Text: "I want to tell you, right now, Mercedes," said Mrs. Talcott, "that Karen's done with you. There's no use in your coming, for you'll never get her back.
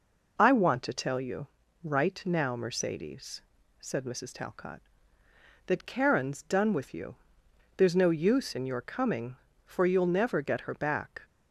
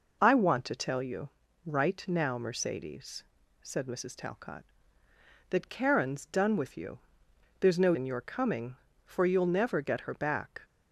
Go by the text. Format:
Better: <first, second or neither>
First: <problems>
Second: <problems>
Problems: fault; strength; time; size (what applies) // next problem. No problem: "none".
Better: first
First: none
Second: skips "use"; at 7.9 s